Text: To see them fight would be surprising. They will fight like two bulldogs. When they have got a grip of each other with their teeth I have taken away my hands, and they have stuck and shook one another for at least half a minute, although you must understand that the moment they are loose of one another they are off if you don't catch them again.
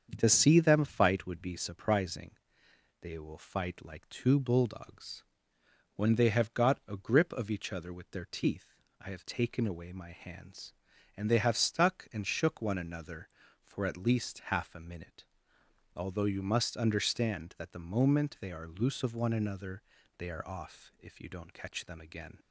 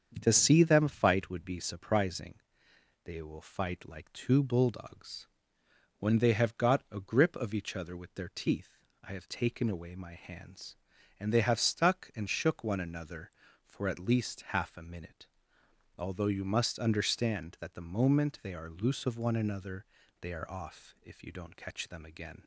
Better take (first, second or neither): neither